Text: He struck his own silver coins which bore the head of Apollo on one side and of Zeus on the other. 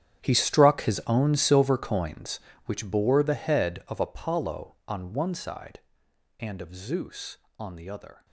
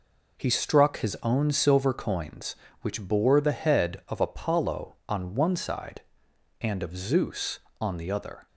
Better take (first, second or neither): second